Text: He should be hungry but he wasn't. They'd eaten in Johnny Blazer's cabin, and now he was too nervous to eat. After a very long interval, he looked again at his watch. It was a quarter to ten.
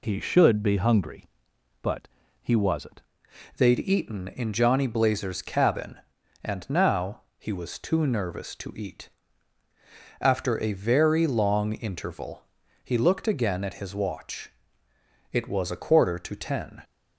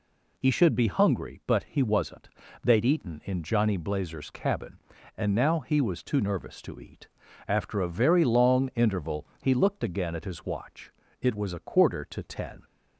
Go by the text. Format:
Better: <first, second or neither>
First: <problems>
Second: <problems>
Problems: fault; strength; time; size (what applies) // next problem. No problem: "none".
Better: second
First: pauses between "but" and "he"; slight; at 2.0 s; 0.34 s long // changes voice at "They'd"; from 3.5 s on; 13.3 s long // pauses between "now" and "he"; slight; at 7.1 s; 0.18 s long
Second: none